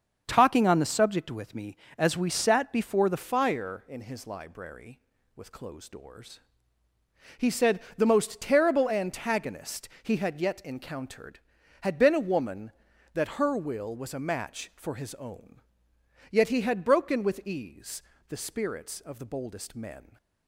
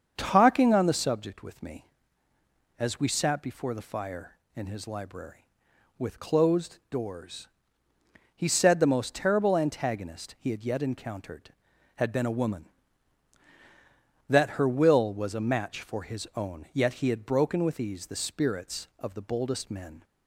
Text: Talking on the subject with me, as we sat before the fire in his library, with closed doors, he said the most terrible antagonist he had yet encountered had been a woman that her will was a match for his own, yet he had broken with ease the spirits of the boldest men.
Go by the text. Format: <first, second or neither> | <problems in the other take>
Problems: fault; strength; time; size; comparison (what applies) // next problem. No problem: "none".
second | starts louder than the rest; until 1.2 s; 7 dB; also in the second // changes voice at "fire"; from 3.1 s on; 17.0 s long // pauses between "said" and "the"; slight; at 7.8 s; 0.16 s long // pauses between "ease" and "the"; slight; at 18.0 s; 0.26 s long